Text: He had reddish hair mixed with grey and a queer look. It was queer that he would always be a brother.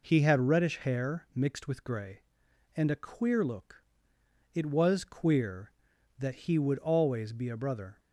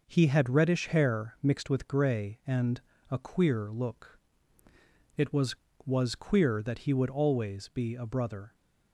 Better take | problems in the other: first | pauses between "and" and "a"; slight; at 2.8 s; 0.28 s long // says "was" twice; at 5.8 s

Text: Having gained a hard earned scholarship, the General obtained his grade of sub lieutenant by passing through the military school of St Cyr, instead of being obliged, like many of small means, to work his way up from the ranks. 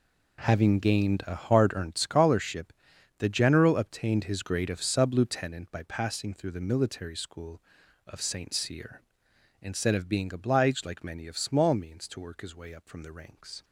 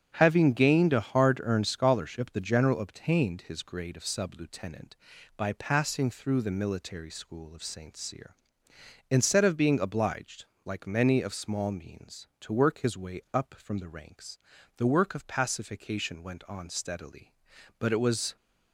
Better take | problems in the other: first | starts louder than the rest; strong; until 1.1 s; 8.5 dB // goes on to say "The work of pacification went on steadily but it was"; strong; from 14.7 s on; 3.5 s long

